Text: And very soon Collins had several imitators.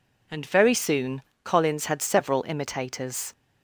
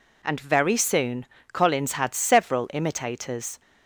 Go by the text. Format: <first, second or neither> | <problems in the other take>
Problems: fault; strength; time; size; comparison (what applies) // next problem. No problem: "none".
neither | pauses between "soon" and "Collins"; slight; the same in both